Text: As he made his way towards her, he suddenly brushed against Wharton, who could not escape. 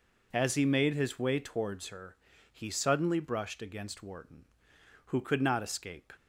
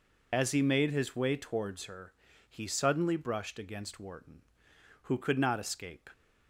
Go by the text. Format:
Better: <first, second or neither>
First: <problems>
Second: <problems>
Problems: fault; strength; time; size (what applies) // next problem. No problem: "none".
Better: first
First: none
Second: loses the start of "As"; at 0.3 s; 35 ms